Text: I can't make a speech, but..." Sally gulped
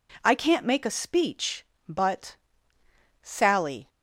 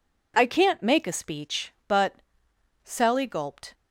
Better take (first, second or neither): second